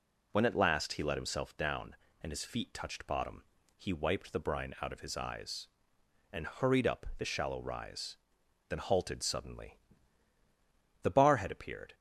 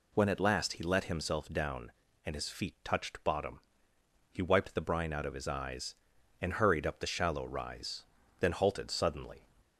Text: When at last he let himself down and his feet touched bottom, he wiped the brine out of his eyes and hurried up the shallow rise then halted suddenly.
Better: second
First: pauses between "rise" and "then"; noticeable; at 8.1 s; 0.52 s long // goes on to say "The bar had appeared"; noticeable; from 11.0 s on; 0.92 s long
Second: pauses between "rise" and "then"; slight; at 8.0 s; 0.36 s long

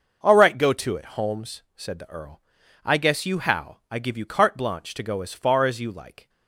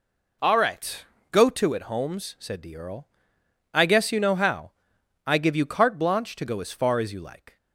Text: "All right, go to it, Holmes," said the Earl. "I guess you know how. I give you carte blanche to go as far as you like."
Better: second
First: starts louder than the rest; noticeable; until 1.3 s; 6 dB // skips "know"; at 3.3 s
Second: none

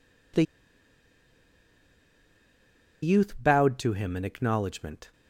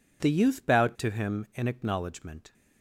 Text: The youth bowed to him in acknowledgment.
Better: second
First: pauses between "The" and "youth"; strong; at 0.4 s; 2.5 s long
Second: none

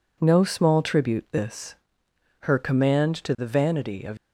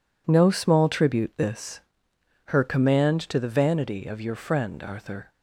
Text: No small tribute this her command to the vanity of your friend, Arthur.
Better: second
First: pauses between "this" and "her"; noticeable; at 1.7 s; 0.66 s long // stops before "your friend Arthur"; at 4.1 s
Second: pauses between "this" and "her"; noticeable; at 1.8 s; 0.66 s long

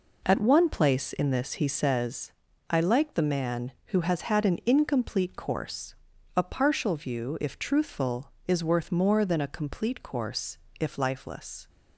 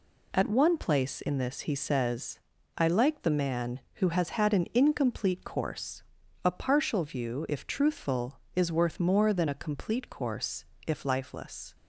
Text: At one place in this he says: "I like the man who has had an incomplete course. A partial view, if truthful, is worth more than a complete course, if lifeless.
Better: second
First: starts louder than the rest; noticeable; until 1.9 s; 4 dB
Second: none

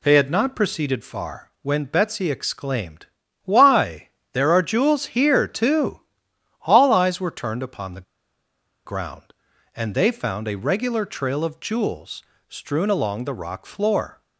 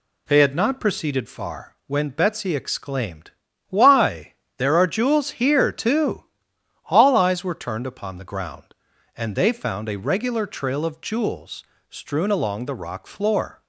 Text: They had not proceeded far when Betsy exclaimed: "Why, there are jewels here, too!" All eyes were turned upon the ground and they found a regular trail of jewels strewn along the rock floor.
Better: second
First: pauses between "the" and "ground"; noticeable; at 8.0 s; 0.83 s long // pauses between "jewels" and "strewn"; slight; at 12.2 s; 0.28 s long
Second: pauses between "jewels" and "strewn"; slight; at 11.6 s; 0.28 s long

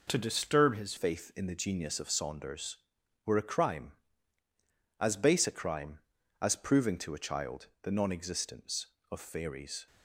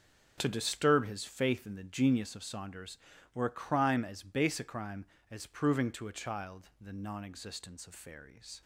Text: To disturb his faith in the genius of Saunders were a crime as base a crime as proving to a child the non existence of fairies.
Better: second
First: changes voice at "faith"; from 0.9 s on; 8.9 s long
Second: none

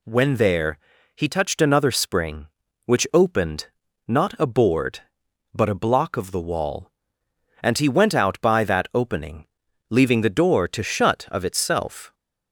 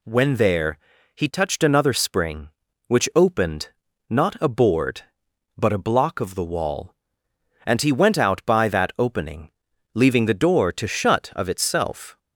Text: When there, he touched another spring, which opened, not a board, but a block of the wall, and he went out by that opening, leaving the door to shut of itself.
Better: neither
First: none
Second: none

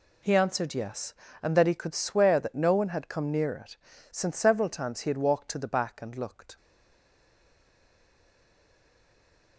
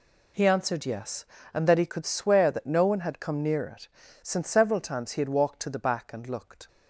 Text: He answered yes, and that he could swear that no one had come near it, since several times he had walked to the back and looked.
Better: second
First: stays silent after the last word; strong; from 6.5 s on; 3.0 s long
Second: none

